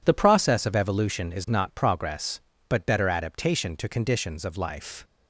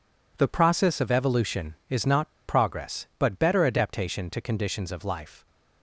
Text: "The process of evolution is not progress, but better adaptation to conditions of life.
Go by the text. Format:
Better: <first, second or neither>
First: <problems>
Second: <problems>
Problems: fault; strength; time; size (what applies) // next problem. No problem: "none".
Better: first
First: none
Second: pauses between "not" and "progress"; slight; at 2.2 s; 0.17 s long